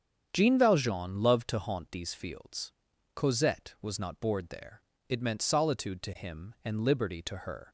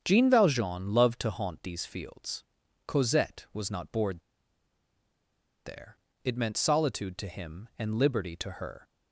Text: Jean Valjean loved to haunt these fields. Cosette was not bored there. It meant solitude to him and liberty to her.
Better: first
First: starts louder than the rest; strong; until 1.3 s; 8 dB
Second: starts louder than the rest; strong; until 1.0 s; 8 dB // pauses between "bored" and "there"; strong; at 4.2 s; 1.4 s long

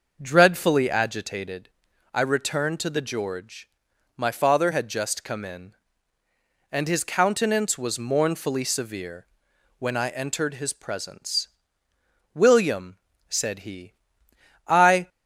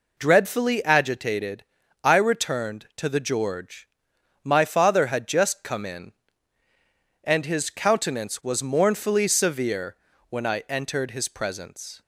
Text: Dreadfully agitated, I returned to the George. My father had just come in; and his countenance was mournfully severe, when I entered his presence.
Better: second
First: starts louder than the rest; noticeable; until 1.2 s; 6 dB // goes on to say "William said he I"; strong; from 12.4 s on; 2.6 s long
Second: none

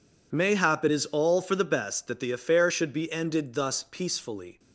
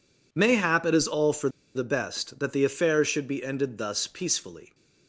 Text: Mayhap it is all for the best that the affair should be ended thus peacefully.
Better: first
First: none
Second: pauses between "for" and "the"; slight; at 1.4 s; 0.26 s long

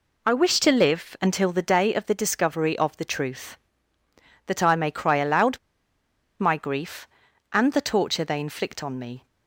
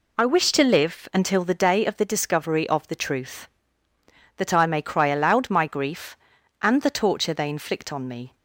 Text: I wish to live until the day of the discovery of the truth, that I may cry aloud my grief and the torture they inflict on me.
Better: second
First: pauses between "aloud" and "my"; noticeable; at 5.5 s; 0.81 s long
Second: none

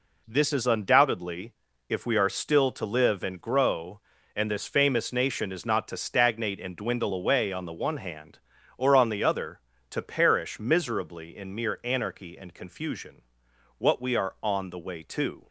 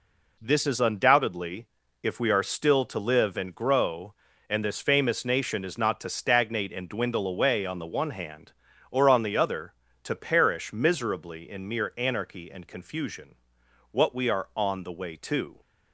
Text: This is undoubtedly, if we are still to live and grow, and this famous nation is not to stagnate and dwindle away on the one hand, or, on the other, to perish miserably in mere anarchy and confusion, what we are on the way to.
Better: neither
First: none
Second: none

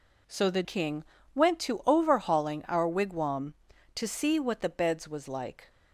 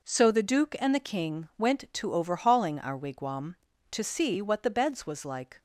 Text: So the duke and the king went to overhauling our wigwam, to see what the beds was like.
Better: second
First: skips "duke and the"; at 0.6 s // pauses between "king" and "went"; slight; at 1.0 s; 0.30 s long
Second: none

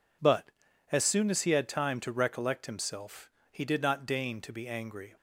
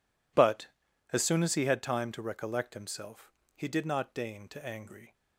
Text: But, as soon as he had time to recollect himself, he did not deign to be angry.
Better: first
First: none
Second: skips "be"; at 4.6 s

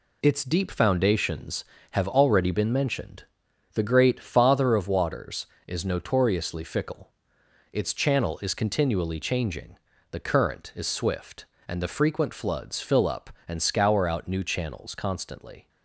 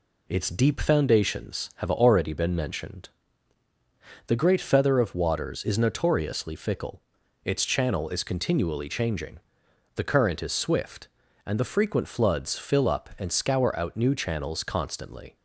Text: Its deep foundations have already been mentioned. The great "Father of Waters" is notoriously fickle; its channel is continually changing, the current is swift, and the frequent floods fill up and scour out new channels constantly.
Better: first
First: none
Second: says "Feather" for "Father"; at 4.5 s

